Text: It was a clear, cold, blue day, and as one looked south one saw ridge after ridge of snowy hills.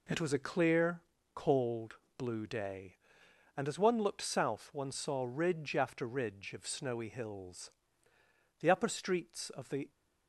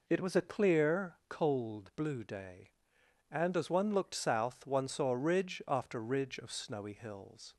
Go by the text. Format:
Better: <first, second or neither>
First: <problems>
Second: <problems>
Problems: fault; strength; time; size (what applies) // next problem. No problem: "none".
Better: second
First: goes on to say "The upper streets of the"; noticeable; from 8.6 s on; 1.2 s long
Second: none